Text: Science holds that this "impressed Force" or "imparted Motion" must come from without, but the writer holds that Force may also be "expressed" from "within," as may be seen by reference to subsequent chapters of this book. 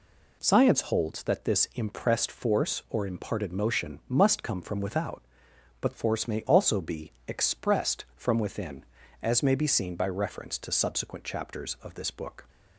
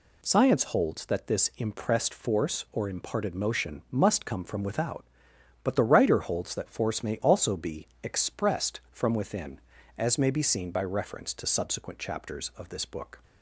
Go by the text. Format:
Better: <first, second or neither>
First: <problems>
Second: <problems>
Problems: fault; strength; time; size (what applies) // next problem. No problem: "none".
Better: second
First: skips "the writer holds that"; at 5.9 s // pauses between "be" and "expressed"; slight; at 7.1 s; 0.16 s long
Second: pauses between "be" and "expressed"; slight; at 7.8 s; 0.16 s long